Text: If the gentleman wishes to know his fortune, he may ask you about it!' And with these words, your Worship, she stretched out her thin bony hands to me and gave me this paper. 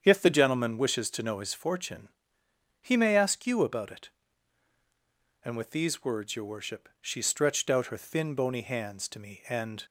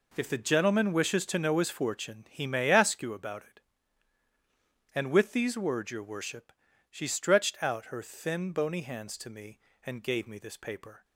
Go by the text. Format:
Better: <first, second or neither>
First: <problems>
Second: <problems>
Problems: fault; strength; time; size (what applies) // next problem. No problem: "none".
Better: second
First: starts louder than the rest; strong; until 1.0 s; 8 dB // stops before "gave me this paper"; at 9.8 s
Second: none